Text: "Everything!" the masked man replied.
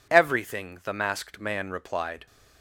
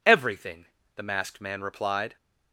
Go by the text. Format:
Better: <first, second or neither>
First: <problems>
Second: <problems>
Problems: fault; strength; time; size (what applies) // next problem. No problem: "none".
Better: neither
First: none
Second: none